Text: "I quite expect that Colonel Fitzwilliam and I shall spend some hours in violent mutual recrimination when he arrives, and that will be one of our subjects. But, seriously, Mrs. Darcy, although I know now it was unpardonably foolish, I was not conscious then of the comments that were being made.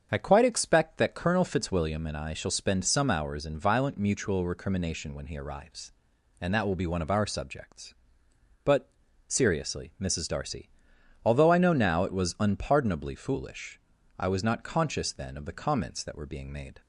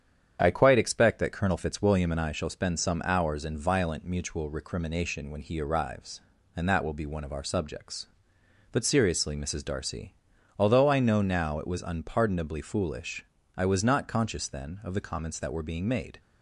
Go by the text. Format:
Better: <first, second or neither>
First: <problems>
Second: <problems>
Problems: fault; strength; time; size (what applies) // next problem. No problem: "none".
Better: neither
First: starts louder than the rest; strong; until 1.1 s; 7 dB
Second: starts louder than the rest; strong; until 1.4 s; 8.5 dB